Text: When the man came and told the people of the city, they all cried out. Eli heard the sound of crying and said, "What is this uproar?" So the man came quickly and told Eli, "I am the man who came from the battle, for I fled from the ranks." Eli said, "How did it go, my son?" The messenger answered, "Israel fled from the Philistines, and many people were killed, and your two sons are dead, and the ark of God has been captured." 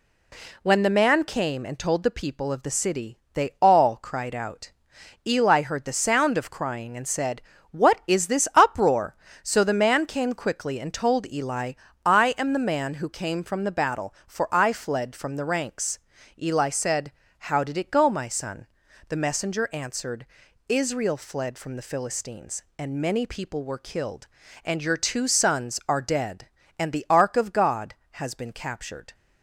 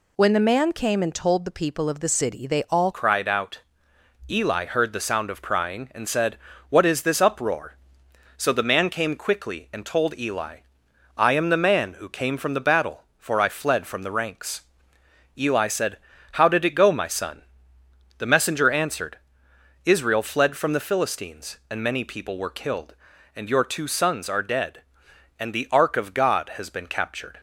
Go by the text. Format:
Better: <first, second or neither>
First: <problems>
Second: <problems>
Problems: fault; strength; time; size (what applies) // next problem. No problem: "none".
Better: first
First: none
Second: changes voice at "cried"; from 2.9 s on; 24.4 s long